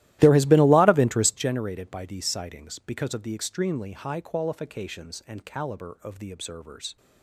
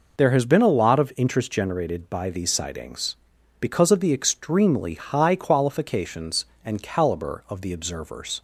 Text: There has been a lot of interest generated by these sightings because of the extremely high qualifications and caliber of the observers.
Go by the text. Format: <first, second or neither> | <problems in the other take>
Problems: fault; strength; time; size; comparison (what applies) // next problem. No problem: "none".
second | starts louder than the rest; strong; until 1.5 s; 15.5 dB